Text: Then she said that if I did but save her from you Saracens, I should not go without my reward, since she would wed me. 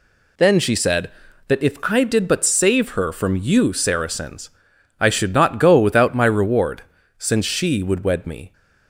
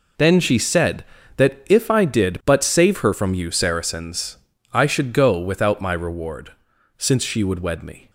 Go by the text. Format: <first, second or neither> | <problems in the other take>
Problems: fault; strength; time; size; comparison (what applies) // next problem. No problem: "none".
first | skips "not"; at 5.1 s